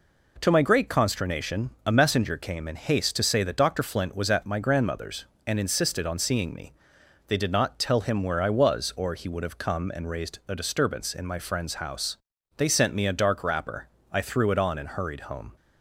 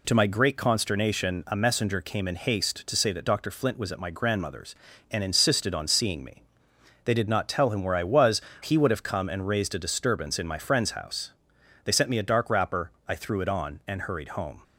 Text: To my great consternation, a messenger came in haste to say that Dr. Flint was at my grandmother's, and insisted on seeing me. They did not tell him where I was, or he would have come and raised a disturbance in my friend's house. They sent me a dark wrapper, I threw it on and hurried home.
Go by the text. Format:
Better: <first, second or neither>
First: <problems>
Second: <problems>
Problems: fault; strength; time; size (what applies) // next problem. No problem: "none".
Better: first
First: none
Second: skips "or"; at 8.5 s